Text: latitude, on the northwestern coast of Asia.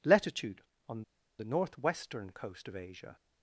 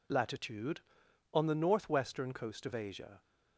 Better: second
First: pauses between "on" and "the"; slight; at 1.0 s; 0.36 s long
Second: none

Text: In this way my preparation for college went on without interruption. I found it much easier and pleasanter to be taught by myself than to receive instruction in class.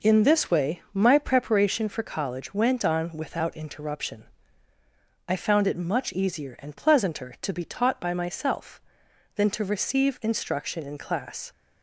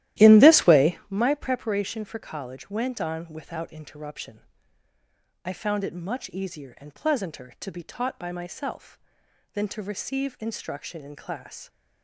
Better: first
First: none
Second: starts louder than the rest; strong; until 1.1 s; 14 dB

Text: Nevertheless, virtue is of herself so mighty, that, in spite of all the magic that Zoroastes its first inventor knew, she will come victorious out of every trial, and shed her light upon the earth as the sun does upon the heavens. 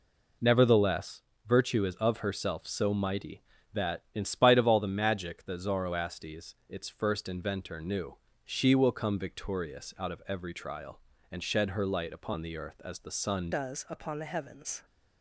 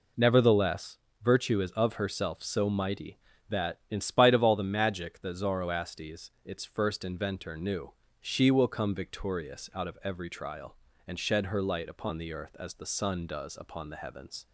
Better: second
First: changes voice at "does"; from 13.5 s on; 1.3 s long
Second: none

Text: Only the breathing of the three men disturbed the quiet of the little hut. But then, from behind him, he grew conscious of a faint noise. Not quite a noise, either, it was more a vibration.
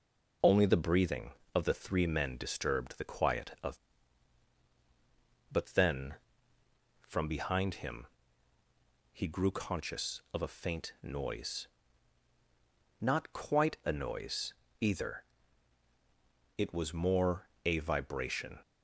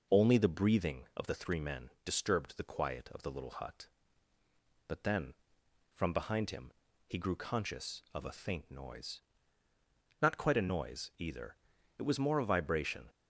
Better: second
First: skips "the little hut"; at 4.6 s // pauses between "more" and "a"; slight; at 17.4 s; 0.18 s long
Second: none

